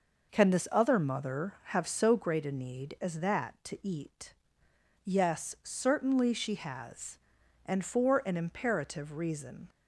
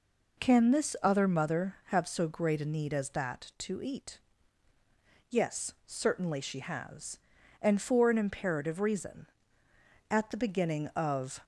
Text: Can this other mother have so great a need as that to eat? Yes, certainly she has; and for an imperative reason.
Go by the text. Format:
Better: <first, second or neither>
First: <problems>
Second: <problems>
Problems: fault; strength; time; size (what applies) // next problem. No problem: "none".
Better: first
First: none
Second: goes on to say "At the beginning of"; noticeable; from 10.1 s on; 1.3 s long